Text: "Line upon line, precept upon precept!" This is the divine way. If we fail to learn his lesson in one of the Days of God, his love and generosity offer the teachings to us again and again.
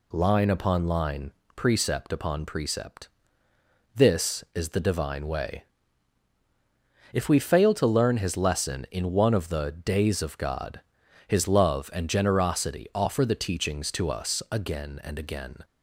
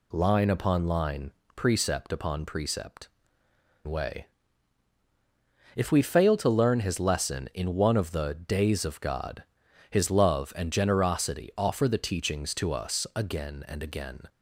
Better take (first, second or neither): first